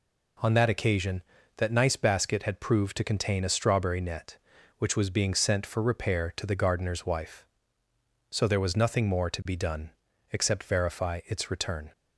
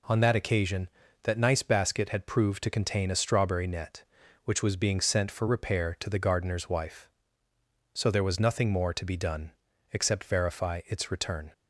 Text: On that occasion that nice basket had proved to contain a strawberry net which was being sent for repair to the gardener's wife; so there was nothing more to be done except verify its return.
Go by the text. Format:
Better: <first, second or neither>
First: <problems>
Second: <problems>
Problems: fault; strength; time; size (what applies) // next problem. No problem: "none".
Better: neither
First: pauses between "done" and "except"; at 9.9 s; 0.40 s long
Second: pauses between "done" and "except"; at 9.5 s; 0.40 s long